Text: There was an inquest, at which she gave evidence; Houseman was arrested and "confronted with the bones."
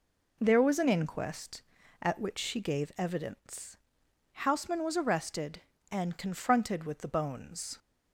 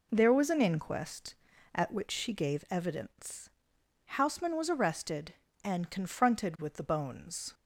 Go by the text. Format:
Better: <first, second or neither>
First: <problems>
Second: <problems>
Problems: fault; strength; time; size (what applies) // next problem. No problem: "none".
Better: neither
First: none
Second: none